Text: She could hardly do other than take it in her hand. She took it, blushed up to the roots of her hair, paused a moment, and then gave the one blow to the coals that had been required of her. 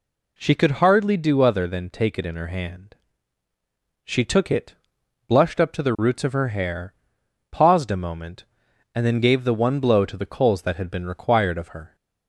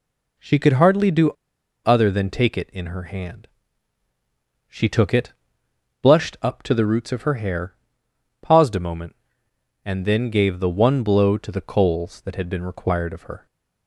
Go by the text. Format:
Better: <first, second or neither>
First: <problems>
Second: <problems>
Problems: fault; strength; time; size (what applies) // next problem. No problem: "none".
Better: first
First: none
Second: pauses between "do" and "other"; noticeable; at 1.3 s; 0.54 s long